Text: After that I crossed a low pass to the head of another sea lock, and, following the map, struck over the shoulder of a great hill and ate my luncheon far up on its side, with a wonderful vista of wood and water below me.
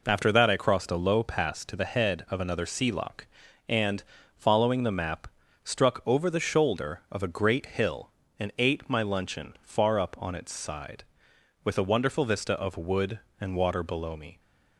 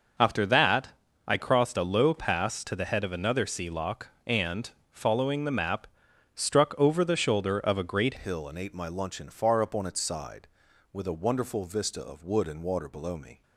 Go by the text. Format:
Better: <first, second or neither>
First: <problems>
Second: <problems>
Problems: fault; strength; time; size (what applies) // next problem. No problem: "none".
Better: first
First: none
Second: starts louder than the rest; until 1.5 s; 6 dB // pauses between "that" and "I"; at 0.8 s; 0.38 s long // changes voice at "hill"; from 8.1 s on; 5.3 s long